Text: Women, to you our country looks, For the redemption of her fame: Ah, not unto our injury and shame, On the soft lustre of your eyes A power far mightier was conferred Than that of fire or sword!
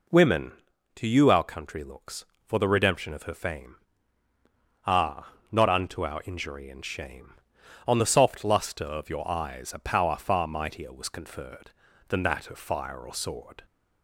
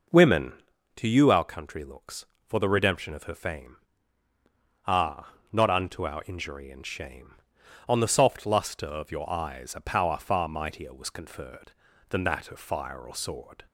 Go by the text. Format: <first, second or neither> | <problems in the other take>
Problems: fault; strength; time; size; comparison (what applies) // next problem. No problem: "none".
first | starts louder than the rest; noticeable; until 1.3 s; 5 dB